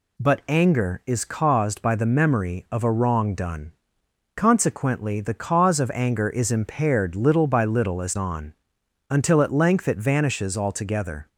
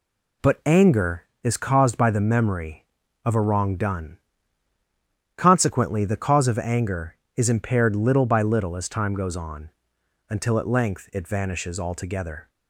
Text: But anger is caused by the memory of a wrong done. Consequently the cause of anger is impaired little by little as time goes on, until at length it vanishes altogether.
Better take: second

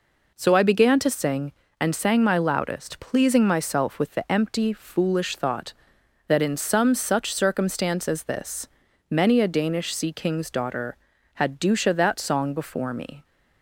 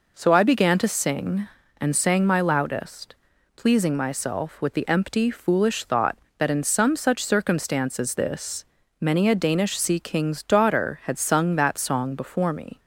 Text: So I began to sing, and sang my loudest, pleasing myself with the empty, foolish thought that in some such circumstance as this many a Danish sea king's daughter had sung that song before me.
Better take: second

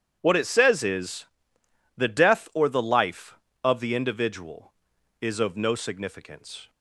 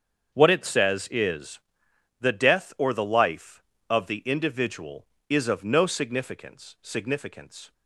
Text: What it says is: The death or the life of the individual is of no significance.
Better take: first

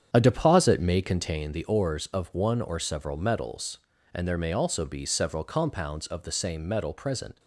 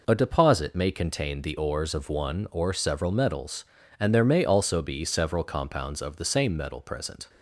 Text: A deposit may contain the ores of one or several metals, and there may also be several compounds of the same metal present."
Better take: second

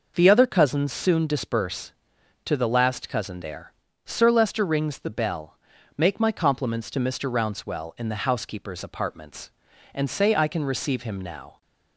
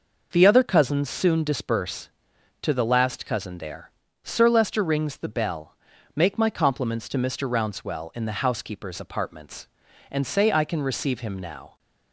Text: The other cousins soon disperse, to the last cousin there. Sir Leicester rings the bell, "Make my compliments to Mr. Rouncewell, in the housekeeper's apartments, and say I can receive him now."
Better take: neither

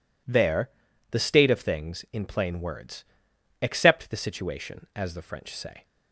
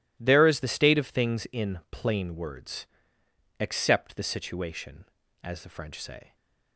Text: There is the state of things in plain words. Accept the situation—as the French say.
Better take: second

